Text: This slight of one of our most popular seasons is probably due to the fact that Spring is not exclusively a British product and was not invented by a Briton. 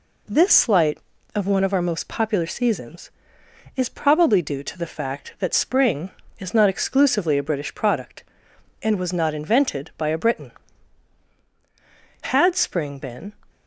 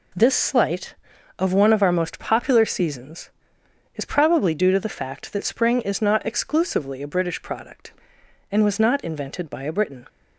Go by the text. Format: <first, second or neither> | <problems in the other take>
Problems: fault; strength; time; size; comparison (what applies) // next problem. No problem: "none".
second | goes on to say "Had Spring been"; noticeable; from 12.2 s on; 1.1 s long